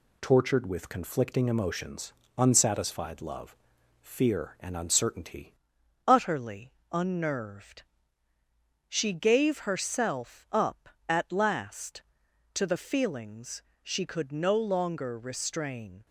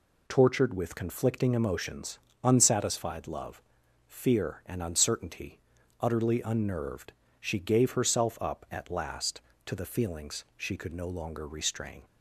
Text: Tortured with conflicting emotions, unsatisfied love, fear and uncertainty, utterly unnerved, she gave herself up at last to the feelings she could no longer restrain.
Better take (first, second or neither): second